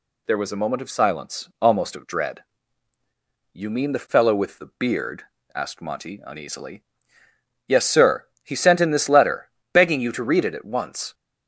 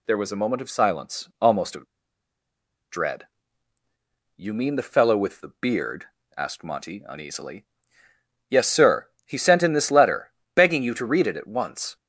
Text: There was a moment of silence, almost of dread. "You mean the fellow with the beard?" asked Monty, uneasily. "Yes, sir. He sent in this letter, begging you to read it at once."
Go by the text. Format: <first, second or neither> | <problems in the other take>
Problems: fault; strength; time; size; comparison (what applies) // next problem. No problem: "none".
first | pauses between "of" and "dread"; at 1.8 s; 1.0 s long